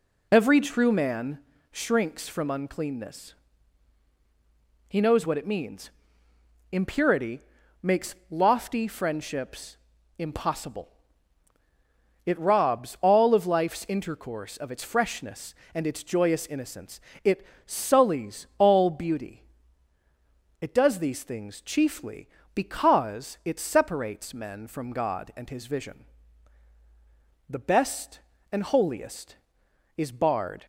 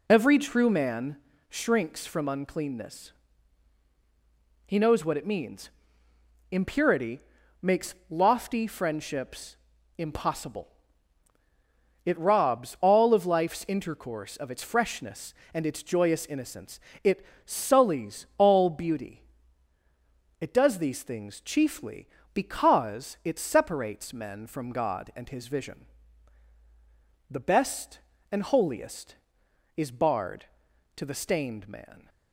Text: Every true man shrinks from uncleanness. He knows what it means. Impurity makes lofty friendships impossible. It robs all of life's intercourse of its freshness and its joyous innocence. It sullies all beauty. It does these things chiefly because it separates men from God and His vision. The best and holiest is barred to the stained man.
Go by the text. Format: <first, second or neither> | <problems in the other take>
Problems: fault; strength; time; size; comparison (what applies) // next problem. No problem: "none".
second | pauses between "man" and "shrinks"; slight; at 1.3 s; 0.32 s long; slight in the second // pauses between "Impurity" and "makes"; at 7.4 s; 0.42 s long; also in the second // pauses between "makes" and "lofty"; slight; at 8.1 s; 0.16 s long; slight in the second // pauses between "friendships" and "impossible"; at 9.7 s; 0.40 s long; also in the second // pauses between "It" and "sullies"; slight; at 17.4 s; 0.22 s long; slight in the second // stops before "to the stained man"; at 30.6 s